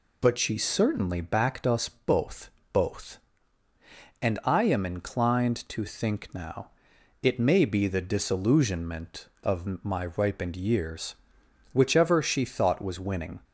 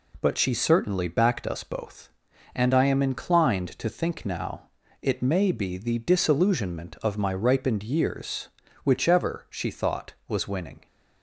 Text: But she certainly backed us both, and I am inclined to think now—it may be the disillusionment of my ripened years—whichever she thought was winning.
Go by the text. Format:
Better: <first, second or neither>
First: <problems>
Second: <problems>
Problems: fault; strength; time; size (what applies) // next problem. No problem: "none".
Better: second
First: says "both" twice; at 2.7 s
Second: none